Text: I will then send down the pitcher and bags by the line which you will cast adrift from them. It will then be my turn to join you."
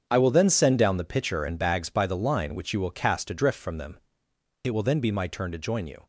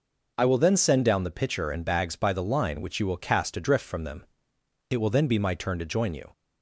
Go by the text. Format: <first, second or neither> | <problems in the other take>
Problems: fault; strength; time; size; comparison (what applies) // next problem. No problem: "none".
second | gets quieter; strong; throughout; 11.5 dB